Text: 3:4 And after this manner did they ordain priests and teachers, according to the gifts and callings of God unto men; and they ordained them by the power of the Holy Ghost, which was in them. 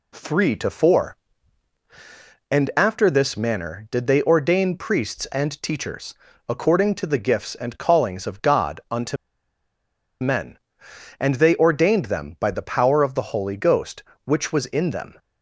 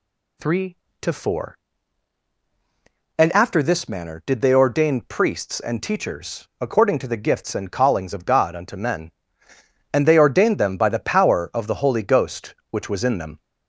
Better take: second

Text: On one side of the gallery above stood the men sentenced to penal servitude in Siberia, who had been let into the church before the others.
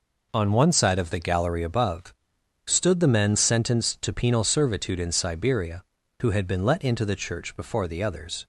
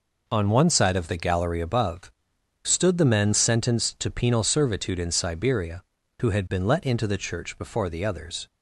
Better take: neither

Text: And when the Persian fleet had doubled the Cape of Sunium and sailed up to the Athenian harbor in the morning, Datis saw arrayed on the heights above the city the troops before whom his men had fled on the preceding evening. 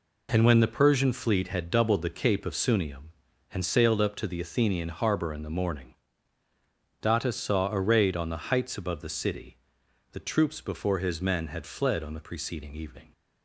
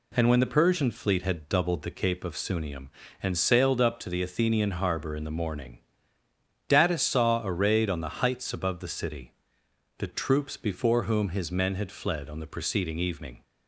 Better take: second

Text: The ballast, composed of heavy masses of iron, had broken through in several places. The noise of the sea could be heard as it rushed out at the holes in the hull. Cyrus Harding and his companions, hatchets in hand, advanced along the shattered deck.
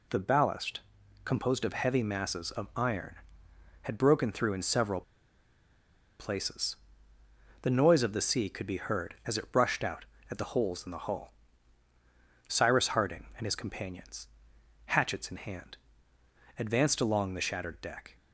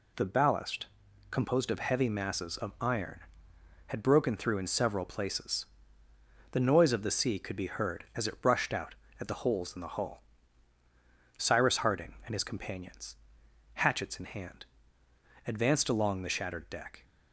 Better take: second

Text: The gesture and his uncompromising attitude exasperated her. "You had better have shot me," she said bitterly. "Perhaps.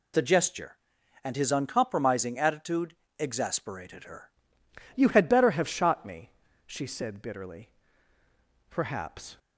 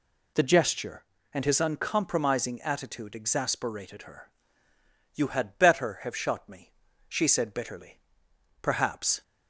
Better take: second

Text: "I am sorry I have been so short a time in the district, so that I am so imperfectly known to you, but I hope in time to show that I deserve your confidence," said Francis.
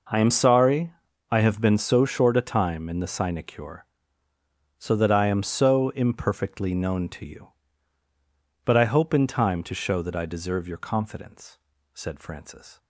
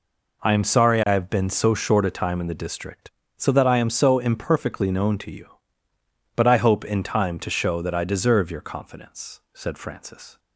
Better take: second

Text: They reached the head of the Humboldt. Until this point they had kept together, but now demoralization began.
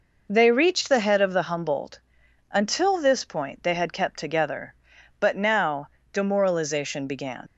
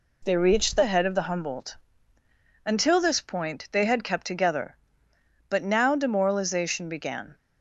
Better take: second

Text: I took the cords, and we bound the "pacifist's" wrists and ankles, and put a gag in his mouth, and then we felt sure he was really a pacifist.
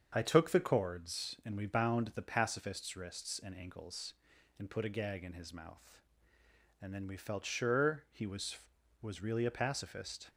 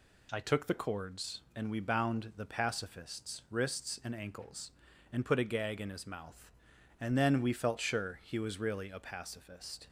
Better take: second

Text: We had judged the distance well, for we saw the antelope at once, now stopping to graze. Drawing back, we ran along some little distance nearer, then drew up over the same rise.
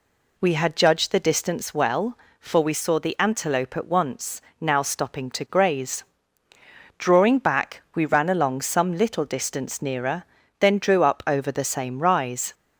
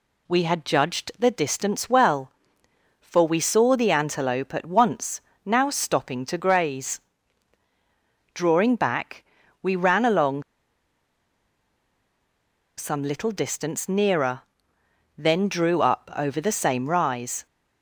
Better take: first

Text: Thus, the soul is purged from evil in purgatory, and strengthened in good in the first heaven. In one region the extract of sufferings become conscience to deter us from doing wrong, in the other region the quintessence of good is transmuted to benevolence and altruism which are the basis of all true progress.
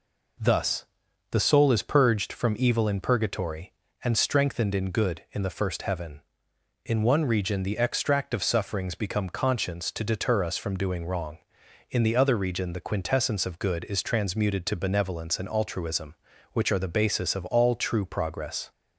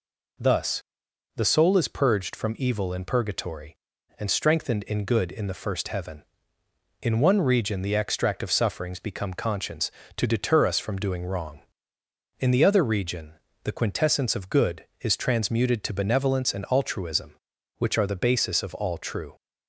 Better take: first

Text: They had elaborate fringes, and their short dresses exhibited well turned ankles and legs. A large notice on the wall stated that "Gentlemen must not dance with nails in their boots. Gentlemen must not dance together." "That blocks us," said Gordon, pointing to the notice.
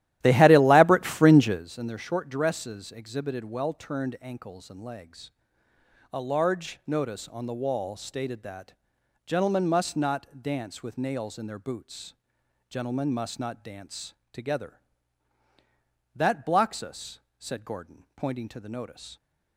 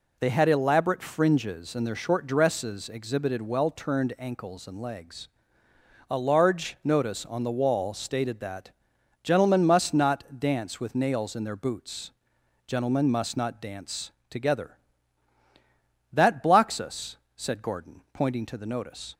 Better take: second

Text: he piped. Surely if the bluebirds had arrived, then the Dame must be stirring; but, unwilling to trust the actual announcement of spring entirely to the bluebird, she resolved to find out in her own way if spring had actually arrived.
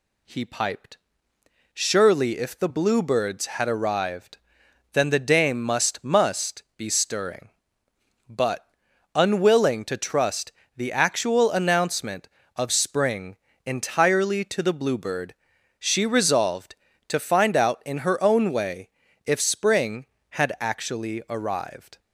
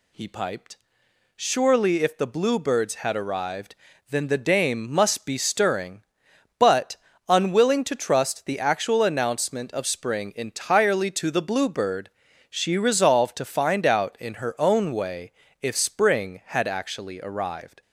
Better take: second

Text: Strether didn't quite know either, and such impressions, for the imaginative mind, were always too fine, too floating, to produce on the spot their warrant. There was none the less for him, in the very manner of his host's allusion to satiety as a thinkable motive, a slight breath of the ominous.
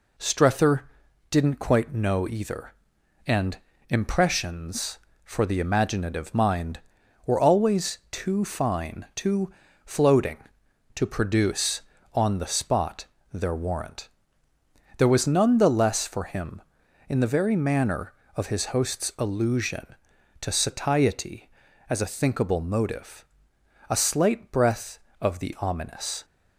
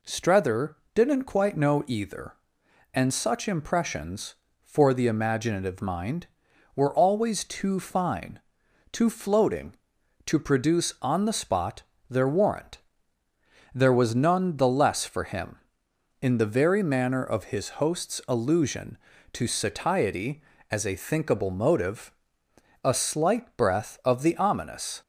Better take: second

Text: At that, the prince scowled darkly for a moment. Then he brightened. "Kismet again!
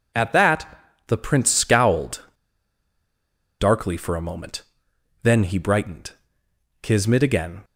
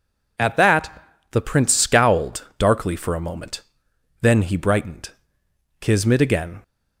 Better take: second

